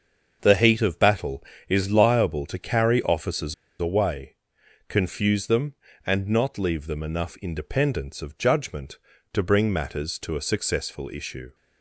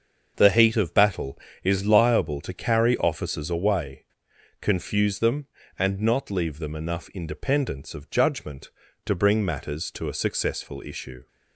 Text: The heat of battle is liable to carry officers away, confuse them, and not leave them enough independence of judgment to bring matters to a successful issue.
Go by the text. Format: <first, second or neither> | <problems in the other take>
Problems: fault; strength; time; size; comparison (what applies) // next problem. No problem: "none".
second | starts louder than the rest; until 1.4 s; 6.5 dB; also in the second // pauses between "officers" and "away"; slight; at 3.5 s; 0.26 s long